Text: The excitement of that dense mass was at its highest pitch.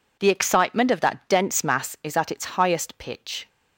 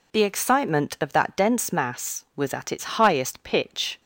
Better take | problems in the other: second | says "is" for "was"; at 2.0 s

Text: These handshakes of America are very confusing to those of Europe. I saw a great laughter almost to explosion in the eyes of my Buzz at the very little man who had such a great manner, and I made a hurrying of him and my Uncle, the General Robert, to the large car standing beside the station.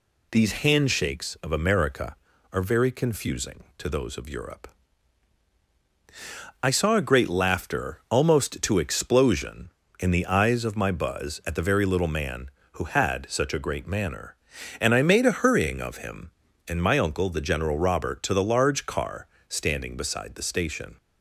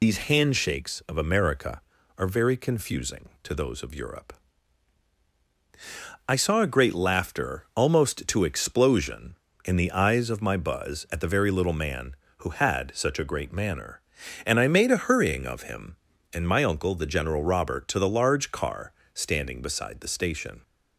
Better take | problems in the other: first | loses the start of "These"; at 0.0 s; 55 ms // pauses between "car" and "standing"; slight; at 18.9 s; 0.22 s long; slight in the first

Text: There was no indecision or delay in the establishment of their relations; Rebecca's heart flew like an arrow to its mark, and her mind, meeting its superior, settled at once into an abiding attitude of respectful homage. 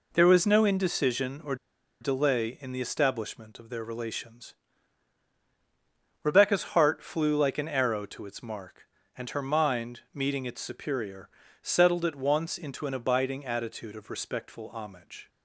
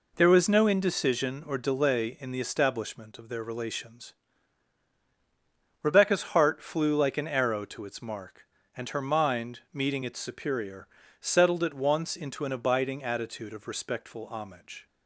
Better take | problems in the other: second | pauses between "or" and "delay"; at 1.5 s; 0.45 s long

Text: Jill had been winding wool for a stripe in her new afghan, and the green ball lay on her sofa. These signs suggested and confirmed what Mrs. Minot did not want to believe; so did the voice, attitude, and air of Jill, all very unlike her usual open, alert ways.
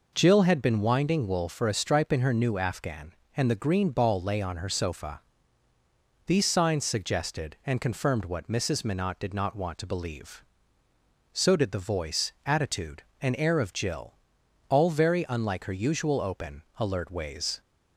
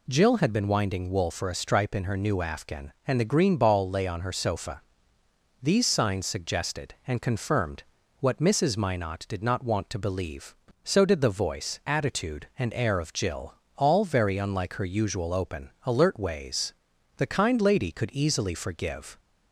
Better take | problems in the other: first | pauses between "confirmed" and "what"; at 7.8 s; 0.38 s long // goes on to say "The kind lady could easily forgive"; strong; from 17.1 s on; 2.0 s long

